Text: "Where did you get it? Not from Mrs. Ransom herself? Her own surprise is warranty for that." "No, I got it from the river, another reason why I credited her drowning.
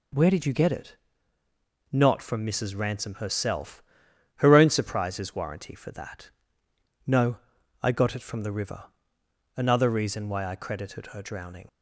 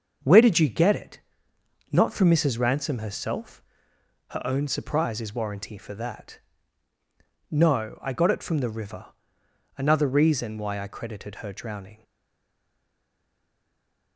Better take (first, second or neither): first